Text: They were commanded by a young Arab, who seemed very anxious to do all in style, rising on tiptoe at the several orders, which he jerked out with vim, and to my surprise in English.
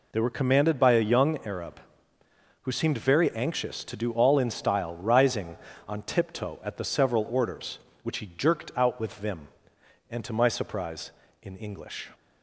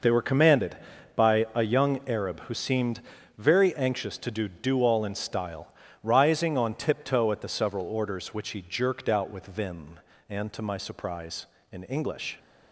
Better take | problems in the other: first | pauses between "seemed" and "very"; at 2.9 s; 0.38 s long // says "do" twice; at 4.4 s

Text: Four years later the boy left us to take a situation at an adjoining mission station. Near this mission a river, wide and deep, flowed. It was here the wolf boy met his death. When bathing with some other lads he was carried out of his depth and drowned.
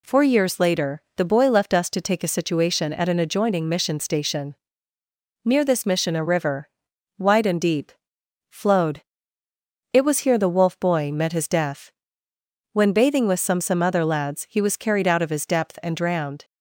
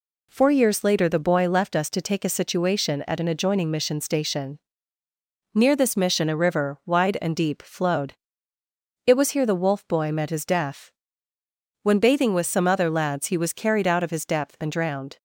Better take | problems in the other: second | pauses between "later" and "the"; slight; at 1.0 s; 0.16 s long // says "some" twice; at 13.6 s

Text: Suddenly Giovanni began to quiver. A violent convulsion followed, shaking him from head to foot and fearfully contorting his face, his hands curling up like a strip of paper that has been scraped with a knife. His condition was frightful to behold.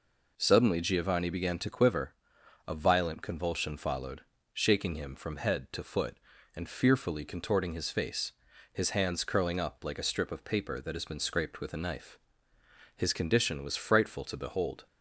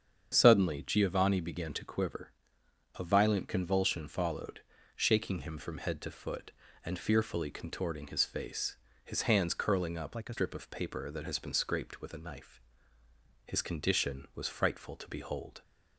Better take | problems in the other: first | starts louder than the rest; strong; until 1.3 s; 7.5 dB // changes voice from "like" to "a"; from 10.1 to 10.3 s; 0.2 s long

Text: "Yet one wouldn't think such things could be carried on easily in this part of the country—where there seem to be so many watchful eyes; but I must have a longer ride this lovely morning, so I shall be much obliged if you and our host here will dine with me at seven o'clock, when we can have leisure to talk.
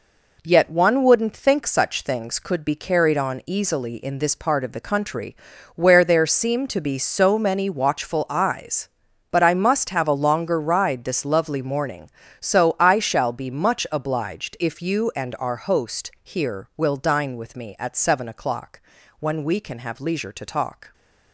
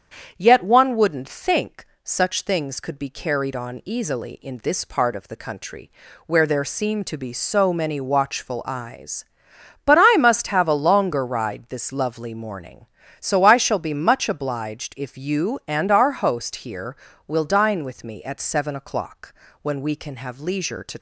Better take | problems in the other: first | starts louder than the rest; strong; until 1.3 s; 8 dB // pauses between "think" and "such"; slight; at 1.8 s; 0.20 s long // stops before "talk"; at 20.9 s

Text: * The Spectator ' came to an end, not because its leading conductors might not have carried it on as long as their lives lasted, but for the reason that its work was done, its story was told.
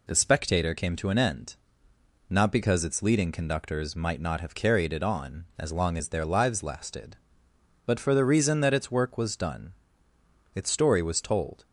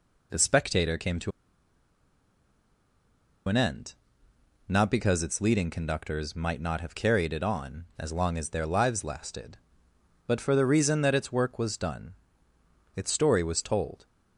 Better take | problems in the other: first | pauses between "to" and "an"; strong; at 1.3 s; 2.1 s long

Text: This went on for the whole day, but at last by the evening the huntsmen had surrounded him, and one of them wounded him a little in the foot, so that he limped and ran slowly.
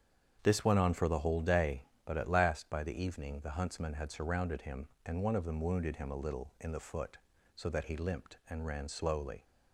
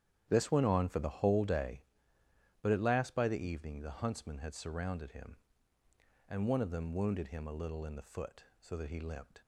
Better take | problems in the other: first | starts louder than the rest; strong; until 1.2 s; 10 dB; strong in the first // stops before "and ran slowly"; at 9.4 s

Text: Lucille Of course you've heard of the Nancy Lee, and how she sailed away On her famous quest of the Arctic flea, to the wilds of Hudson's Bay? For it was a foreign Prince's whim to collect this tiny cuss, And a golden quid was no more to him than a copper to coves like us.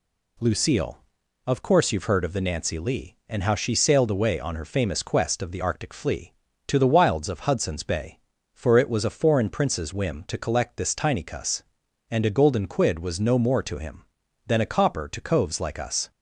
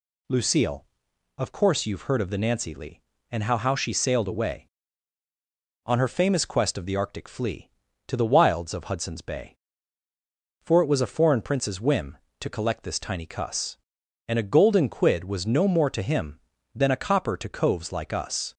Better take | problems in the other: first | says "how" twice; at 3.5 s

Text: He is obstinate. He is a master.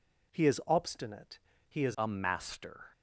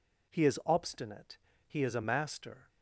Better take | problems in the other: second | changes voice at "a"; from 1.9 s on; 0.9 s long

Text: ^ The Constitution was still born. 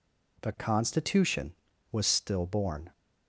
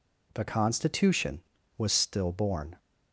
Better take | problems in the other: neither | none

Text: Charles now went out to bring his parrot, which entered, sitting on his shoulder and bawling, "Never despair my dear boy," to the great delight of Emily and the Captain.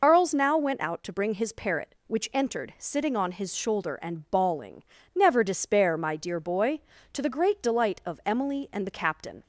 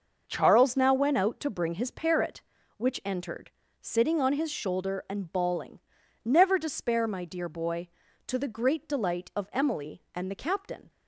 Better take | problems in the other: second | loses the start of "Charles"; at 0.0 s; 125 ms

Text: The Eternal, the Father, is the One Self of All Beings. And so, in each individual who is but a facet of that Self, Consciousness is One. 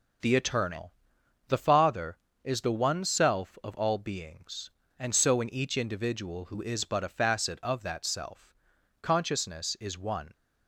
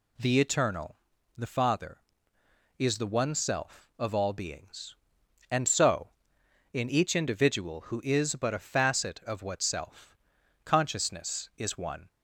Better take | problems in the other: first | says "what" for "that"; at 9.4 s

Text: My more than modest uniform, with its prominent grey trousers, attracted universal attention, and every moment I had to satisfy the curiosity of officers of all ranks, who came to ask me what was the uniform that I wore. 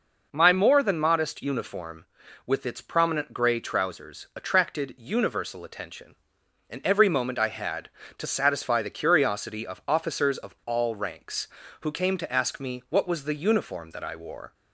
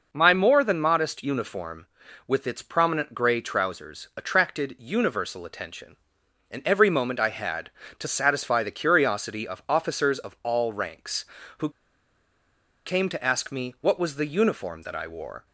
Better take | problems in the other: first | pauses between "who" and "came"; at 11.6 s; 1.1 s long

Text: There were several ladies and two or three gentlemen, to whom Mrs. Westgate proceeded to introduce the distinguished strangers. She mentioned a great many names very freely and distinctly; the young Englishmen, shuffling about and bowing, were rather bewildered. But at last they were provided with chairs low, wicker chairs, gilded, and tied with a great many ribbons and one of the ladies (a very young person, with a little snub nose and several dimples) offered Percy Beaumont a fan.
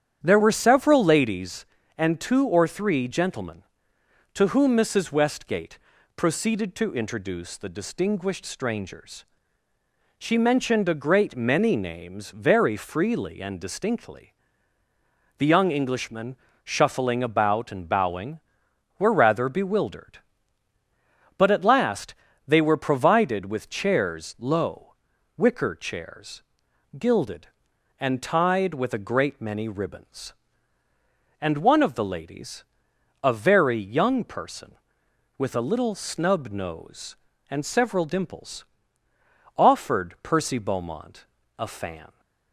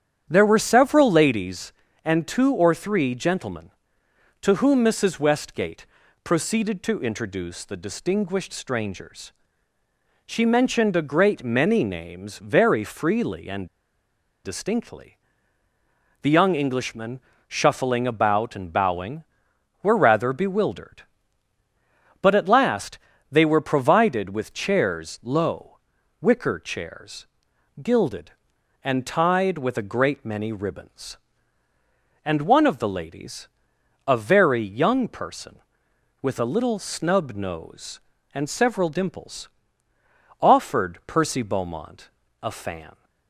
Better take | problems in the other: first | starts louder than the rest; strong; until 1.3 s; 9 dB; strong in the first // pauses between "Westgate" and "proceeded"; at 5.8 s; 0.40 s long; also in the first // pauses between "and" and "distinctly"; noticeable; at 13.6 s; 0.78 s long // pauses between "last" and "they"; slight; at 22.9 s; 0.32 s long; slight in the first // pauses between "Beaumont" and "a"; slight; at 42.0 s; 0.32 s long; slight in the first

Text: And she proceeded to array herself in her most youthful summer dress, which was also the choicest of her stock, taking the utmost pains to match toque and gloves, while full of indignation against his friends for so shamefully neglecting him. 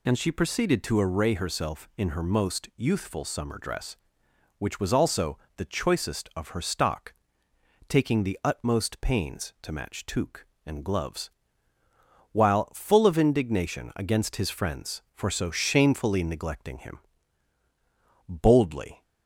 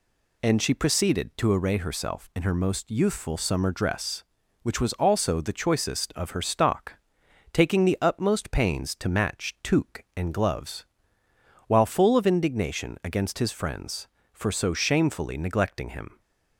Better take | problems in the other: second | pauses between "also" and "the"; slight; at 5.3 s; 0.20 s long // goes on to say "Boldly"; noticeable; from 18.2 s on; 0.74 s long

